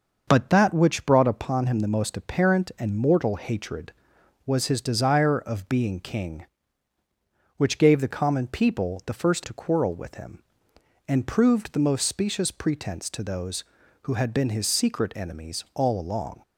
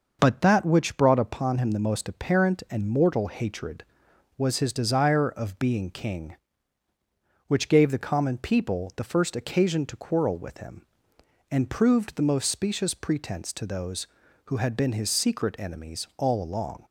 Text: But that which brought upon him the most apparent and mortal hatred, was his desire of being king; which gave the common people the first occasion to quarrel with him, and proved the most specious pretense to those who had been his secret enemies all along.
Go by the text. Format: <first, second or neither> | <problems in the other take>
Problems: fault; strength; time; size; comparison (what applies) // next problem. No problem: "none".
second | starts louder than the rest; until 1.2 s; 6.5 dB; also in the second // skips "occasion"; at 9.4 s